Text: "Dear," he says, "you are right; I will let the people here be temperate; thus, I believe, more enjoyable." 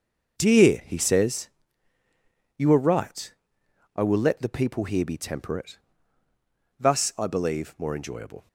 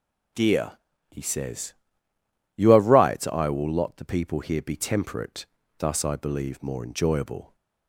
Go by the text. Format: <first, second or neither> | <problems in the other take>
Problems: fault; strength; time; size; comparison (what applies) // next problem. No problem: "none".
first | says "lot" for "let"; at 3.7 s